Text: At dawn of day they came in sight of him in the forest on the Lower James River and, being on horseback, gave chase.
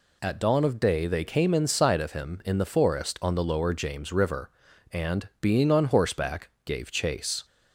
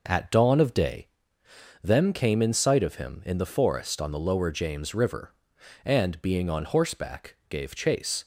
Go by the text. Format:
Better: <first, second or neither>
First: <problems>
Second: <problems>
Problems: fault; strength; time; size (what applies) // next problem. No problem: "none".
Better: first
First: none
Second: says "them" for "they"; at 1.8 s